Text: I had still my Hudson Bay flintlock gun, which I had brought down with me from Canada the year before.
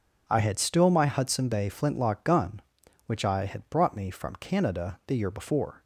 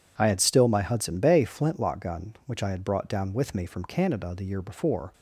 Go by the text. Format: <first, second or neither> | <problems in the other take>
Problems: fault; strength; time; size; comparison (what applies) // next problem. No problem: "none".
second | skips "down with"; at 3.9 s